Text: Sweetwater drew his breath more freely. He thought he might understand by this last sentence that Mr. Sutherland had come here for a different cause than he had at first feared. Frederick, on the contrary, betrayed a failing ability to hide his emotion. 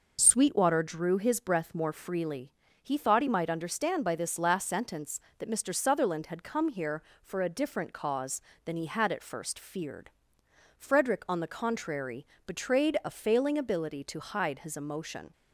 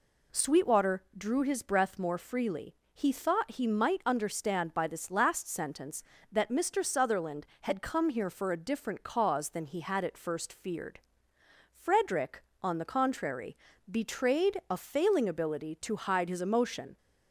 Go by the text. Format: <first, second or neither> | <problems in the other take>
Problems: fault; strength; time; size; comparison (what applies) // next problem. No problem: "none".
neither | none